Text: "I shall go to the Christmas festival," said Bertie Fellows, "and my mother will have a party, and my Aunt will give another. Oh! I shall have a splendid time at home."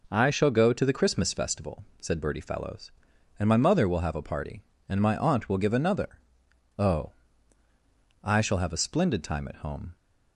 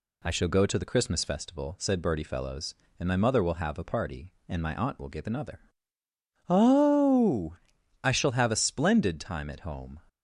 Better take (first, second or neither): neither